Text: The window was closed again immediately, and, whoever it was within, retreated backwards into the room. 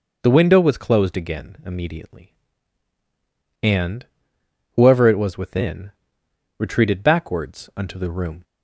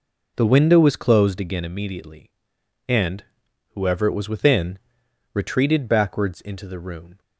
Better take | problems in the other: second | says "unto" for "into"; at 7.7 s

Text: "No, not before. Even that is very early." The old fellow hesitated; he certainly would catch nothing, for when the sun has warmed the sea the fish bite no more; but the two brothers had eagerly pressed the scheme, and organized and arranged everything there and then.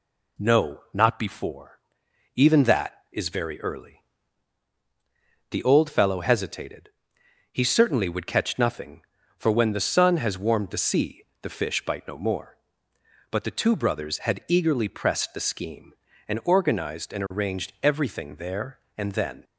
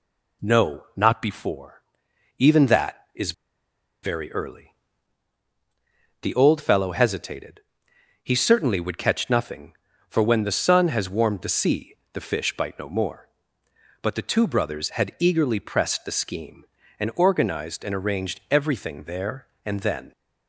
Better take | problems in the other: first | pauses between "is" and "very"; noticeable; at 3.3 s; 0.70 s long // pauses between "sea" and "the"; slight; at 11.9 s; 0.16 s long; slight in the first

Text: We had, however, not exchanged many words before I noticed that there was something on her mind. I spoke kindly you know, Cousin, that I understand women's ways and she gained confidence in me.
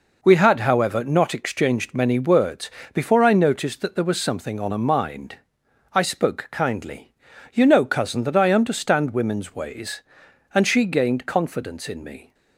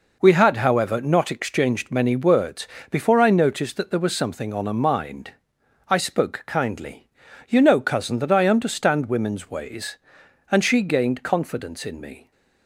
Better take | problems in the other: neither | pauses between "words" and "before"; slight; the same in both // pauses between "kindly" and "you"; noticeable; the same in both

